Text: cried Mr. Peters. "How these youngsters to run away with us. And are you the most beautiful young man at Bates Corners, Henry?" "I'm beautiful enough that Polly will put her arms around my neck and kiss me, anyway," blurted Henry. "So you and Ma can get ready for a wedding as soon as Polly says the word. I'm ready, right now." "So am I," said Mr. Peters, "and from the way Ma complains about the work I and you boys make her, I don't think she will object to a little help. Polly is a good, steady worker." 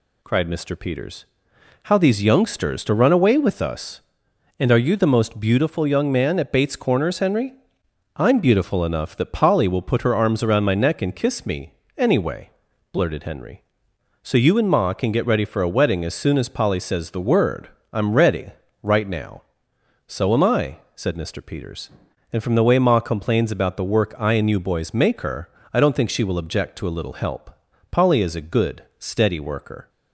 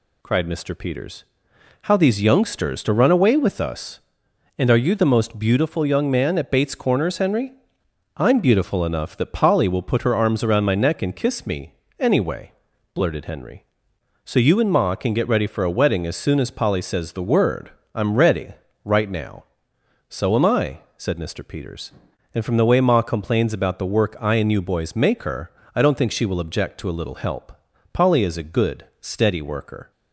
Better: neither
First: none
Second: none

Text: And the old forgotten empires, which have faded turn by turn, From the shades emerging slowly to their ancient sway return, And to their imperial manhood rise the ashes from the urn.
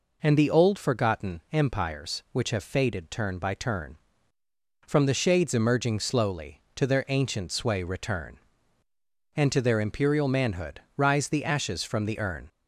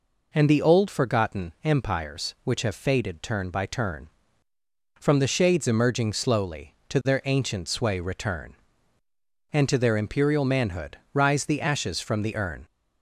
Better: neither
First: pauses between "manhood" and "rise"; slight; at 10.8 s; 0.16 s long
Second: pauses between "manhood" and "rise"; slight; at 10.9 s; 0.16 s long

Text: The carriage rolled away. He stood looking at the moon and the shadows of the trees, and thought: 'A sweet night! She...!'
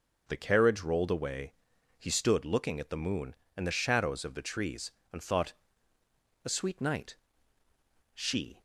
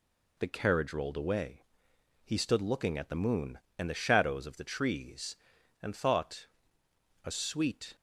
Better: first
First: none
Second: stops before "night She"; at 7.9 s

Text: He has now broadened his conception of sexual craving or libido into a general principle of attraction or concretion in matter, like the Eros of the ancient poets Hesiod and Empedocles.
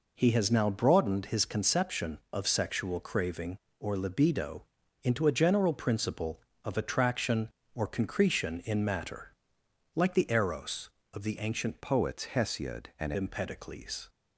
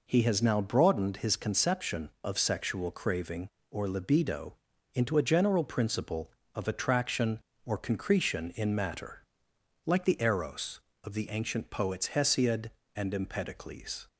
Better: second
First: pauses between "libido" and "into"; at 4.6 s; 0.40 s long // changes voice from "poets" to "and"; from 11.8 to 13.1 s; 1.3 s long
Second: pauses between "libido" and "into"; at 4.5 s; 0.40 s long

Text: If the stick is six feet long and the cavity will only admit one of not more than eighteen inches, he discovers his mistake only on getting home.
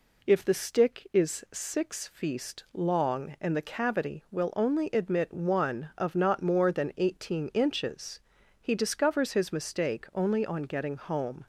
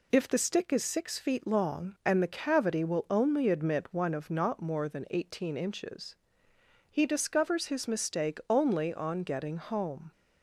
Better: second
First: says "feast" for "feet"; at 2.0 s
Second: none

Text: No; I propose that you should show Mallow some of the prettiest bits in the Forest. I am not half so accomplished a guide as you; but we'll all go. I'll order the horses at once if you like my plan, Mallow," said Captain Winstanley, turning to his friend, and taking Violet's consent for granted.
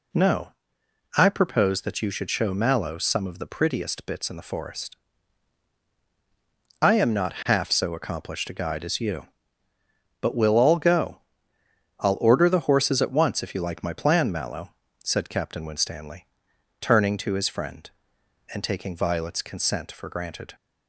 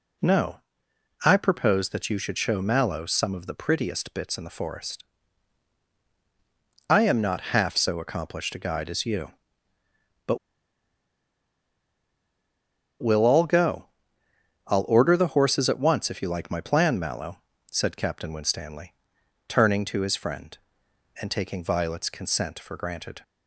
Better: first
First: none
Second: pauses between "but" and "we'll"; strong; at 10.3 s; 2.6 s long

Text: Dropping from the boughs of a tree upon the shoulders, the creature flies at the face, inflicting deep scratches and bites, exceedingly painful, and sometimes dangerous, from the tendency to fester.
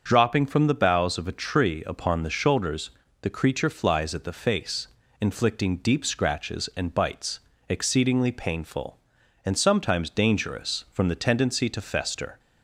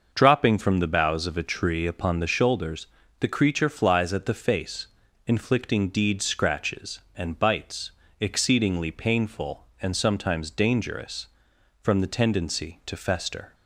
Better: first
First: starts louder than the rest; until 1.1 s; 6.5 dB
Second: starts louder than the rest; noticeable; until 1.1 s; 6 dB // says "deed" for "deep"; at 5.8 s

